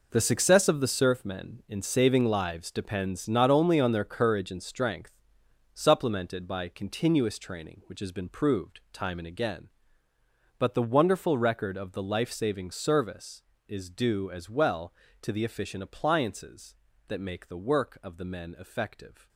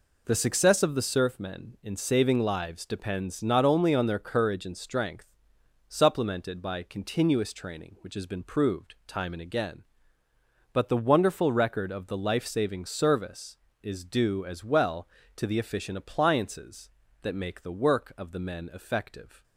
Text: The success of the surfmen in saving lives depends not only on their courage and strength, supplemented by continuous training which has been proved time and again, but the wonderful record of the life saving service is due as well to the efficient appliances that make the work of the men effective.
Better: second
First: gets quieter; strong; throughout; 11.5 dB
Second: none

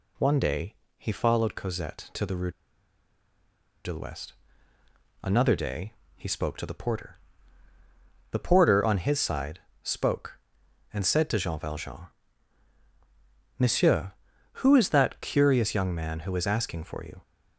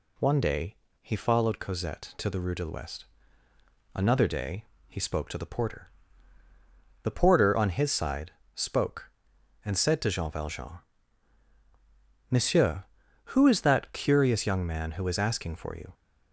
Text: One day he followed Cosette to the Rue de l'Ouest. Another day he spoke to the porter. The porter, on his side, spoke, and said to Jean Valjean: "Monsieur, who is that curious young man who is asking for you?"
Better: second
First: pauses between "day" and "he"; slight; at 0.7 s; 0.22 s long // pauses between "Rue" and "de"; strong; at 2.5 s; 1.3 s long // pauses between "day" and "he"; slight; at 5.9 s; 0.24 s long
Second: pauses between "day" and "he"; slight; at 0.7 s; 0.25 s long // pauses between "day" and "he"; slight; at 4.6 s; 0.24 s long

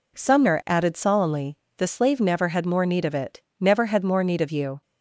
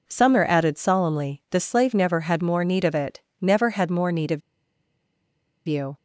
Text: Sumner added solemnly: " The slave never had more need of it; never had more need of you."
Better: first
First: none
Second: pauses between "of" and "you"; strong; at 4.4 s; 1.2 s long

